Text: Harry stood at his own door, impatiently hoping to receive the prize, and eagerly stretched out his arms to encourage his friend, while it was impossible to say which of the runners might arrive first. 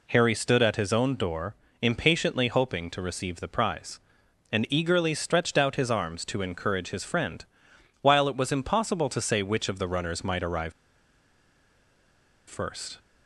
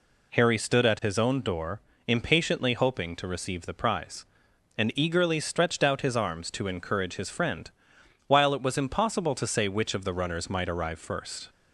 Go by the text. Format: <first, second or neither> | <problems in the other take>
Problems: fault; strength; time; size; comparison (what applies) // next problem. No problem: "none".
second | pauses between "arrive" and "first"; strong; at 10.7 s; 1.7 s long